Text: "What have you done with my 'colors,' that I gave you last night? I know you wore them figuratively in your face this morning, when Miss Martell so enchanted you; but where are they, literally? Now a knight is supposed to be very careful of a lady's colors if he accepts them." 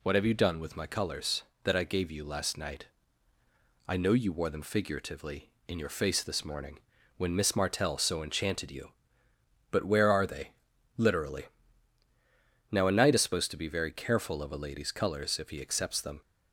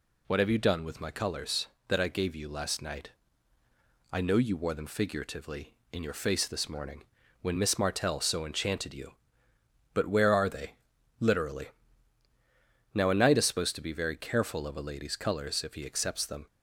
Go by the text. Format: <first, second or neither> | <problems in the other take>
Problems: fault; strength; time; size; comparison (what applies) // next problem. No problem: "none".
neither | none